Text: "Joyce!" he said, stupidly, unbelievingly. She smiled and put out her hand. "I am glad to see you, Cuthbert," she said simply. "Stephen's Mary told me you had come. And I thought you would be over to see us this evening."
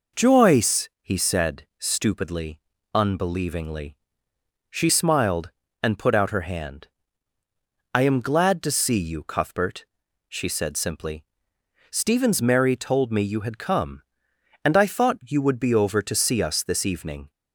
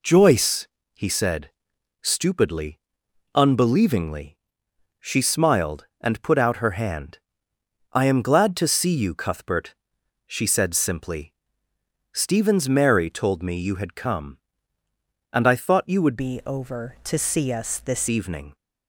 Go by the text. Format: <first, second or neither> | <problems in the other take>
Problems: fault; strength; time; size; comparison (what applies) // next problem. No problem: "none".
first | changes voice from "be" to "this"; from 16.1 to 18.0 s; 1.9 s long